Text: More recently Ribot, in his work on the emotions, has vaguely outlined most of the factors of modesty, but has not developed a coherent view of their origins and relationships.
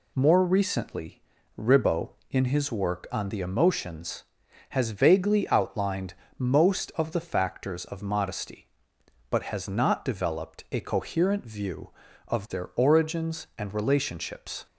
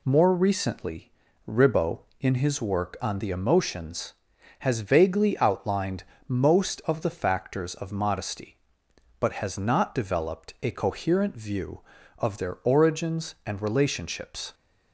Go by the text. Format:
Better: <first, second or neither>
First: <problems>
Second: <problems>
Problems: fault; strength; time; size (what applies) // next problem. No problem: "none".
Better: neither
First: pauses between "recently" and "Ribot"; slight; at 1.2 s; 0.34 s long // pauses between "outlined" and "most"; slight; at 6.1 s; 0.22 s long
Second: pauses between "recently" and "Ribot"; slight; at 1.1 s; 0.34 s long // pauses between "outlined" and "most"; slight; at 6.0 s; 0.22 s long